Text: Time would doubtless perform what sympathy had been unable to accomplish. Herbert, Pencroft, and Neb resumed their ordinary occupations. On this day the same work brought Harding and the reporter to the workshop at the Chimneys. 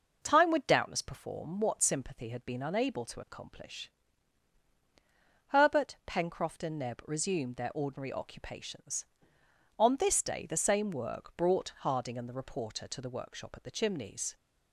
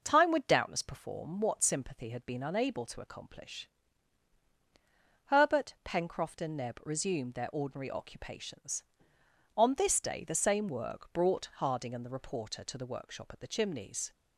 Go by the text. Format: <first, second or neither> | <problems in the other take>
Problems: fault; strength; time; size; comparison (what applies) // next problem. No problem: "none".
neither | none